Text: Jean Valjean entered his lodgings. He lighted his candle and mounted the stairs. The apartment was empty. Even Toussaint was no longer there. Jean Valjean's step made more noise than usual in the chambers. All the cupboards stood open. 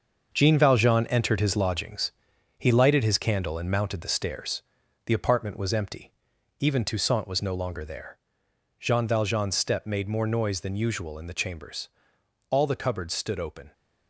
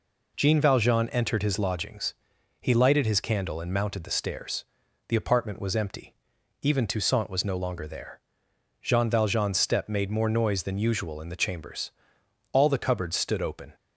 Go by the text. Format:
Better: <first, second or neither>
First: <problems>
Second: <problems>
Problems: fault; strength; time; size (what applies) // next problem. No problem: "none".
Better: second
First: gets quieter; strong; throughout; 9 dB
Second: none